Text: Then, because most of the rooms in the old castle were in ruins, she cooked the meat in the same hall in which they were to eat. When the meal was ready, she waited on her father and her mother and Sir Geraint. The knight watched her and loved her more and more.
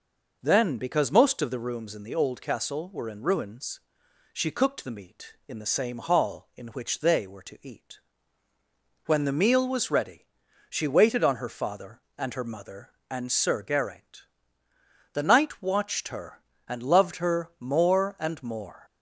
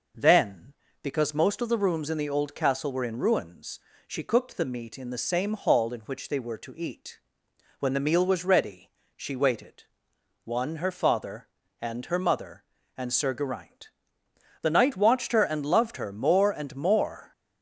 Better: first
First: none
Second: says "one" for "on"; at 10.4 s

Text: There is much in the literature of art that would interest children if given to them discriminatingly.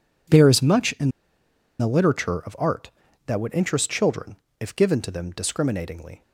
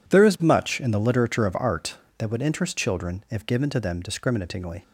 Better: second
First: pauses between "in" and "the"; noticeable; at 1.0 s; 0.70 s long // pauses between "children" and "if"; slight; at 4.3 s; 0.22 s long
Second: none

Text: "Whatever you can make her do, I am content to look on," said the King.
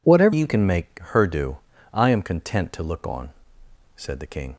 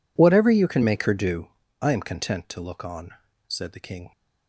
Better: second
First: changes voice at "you"; from 0.3 s on; 4.2 s long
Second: none

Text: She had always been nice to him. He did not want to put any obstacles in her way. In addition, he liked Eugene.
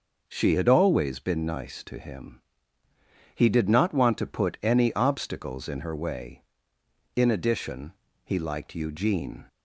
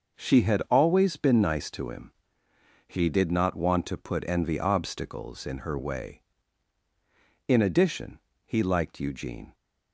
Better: first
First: none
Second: starts louder than the rest; noticeable; until 1.2 s; 6 dB // says "envy" for "any"; at 4.2 s

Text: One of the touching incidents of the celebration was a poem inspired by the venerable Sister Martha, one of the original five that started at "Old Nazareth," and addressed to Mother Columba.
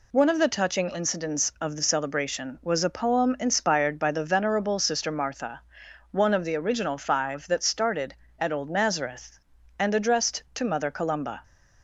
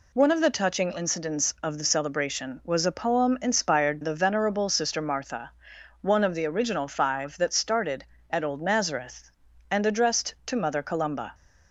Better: first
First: none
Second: skips "by"; at 3.9 s

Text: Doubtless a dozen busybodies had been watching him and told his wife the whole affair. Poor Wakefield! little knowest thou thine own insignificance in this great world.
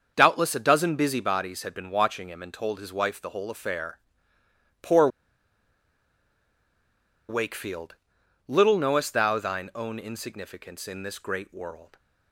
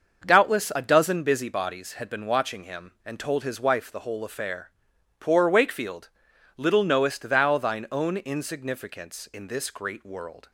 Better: second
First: starts louder than the rest; until 1.1 s; 7 dB // pauses between "Poor" and "Wakefield"; strong; at 5.0 s; 2.2 s long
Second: starts louder than the rest; until 1.3 s; 6.5 dB

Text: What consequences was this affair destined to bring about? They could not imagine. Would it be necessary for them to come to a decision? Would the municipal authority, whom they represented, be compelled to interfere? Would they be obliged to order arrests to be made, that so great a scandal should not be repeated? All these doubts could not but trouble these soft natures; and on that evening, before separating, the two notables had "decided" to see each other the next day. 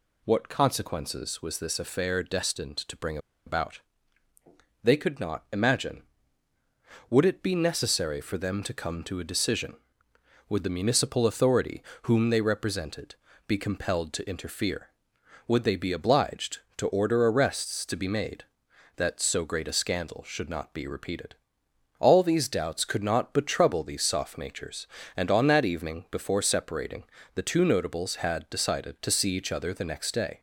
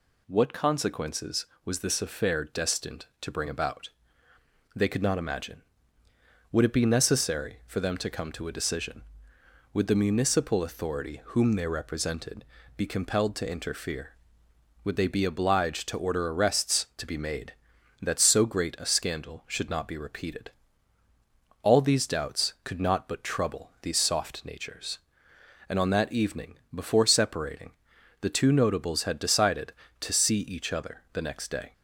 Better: second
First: pauses between "bring" and "about"; slight; at 3.1 s; 0.28 s long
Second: none

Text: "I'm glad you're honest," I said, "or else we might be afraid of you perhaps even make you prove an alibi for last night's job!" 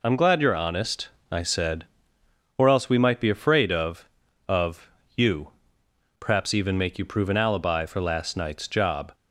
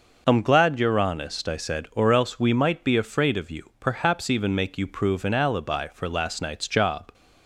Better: second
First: says "of" twice; at 4.4 s // pauses between "you" and "perhaps"; noticeable; at 5.5 s; 0.66 s long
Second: none

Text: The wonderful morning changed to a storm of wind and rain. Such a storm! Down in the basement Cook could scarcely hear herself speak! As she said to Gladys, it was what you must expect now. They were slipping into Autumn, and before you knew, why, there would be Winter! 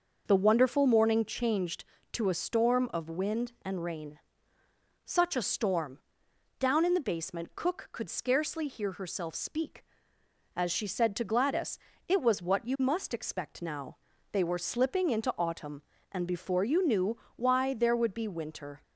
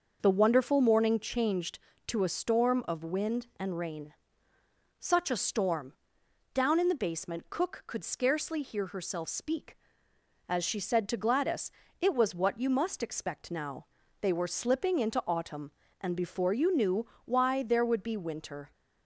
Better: neither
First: starts louder than the rest; noticeable; until 1.2 s; 6 dB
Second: starts louder than the rest; noticeable; until 1.2 s; 6 dB

